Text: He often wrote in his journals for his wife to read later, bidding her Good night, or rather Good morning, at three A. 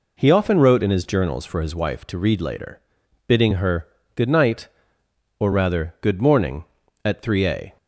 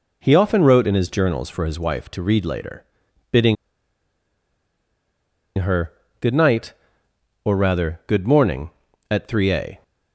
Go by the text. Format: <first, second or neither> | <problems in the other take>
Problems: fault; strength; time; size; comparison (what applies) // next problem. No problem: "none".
first | pauses between "bidding" and "her"; strong; at 3.5 s; 2.0 s long // pauses between "her" and "Good"; slight; at 5.9 s; 0.30 s long; slight in the first